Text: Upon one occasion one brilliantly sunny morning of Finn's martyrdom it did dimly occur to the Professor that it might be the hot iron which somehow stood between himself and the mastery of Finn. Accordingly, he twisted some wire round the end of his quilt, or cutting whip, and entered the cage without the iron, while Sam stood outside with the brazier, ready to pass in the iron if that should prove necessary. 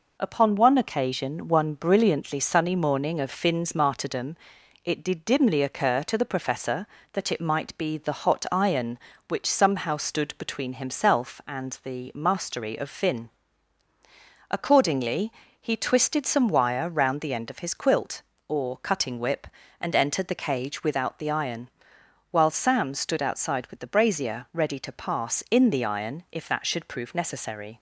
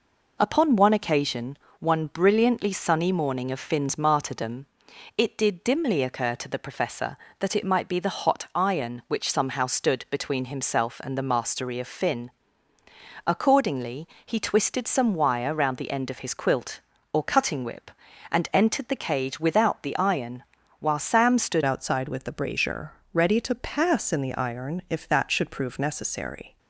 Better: first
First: pauses between "martyrdom" and "it"; noticeable; at 4.3 s; 0.48 s long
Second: pauses between "occasion" and "one"; slight; at 1.5 s; 0.24 s long // pauses between "martyrdom" and "it"; noticeable; at 4.6 s; 0.50 s long // changes voice at "outside"; from 21.6 s on; 4.9 s long

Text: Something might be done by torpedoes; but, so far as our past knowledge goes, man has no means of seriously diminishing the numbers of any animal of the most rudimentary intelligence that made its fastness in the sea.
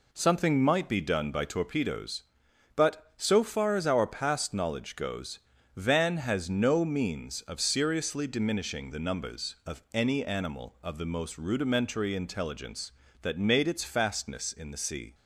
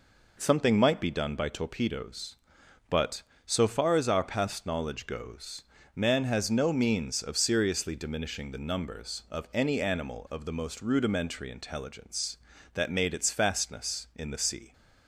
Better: second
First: says "van" for "man"; at 5.7 s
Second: none

